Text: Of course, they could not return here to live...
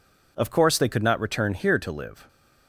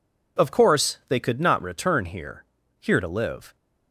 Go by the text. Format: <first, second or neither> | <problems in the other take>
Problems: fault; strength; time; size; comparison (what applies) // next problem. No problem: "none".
first | says "here" twice; at 2.7 s